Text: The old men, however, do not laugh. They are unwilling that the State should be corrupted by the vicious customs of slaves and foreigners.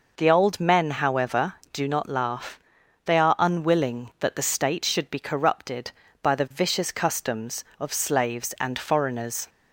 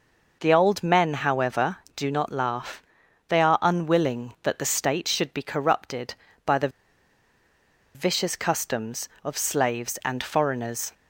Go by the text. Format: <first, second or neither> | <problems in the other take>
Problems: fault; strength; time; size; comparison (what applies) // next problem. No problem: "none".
first | pauses between "the" and "vicious"; strong; at 6.6 s; 1.2 s long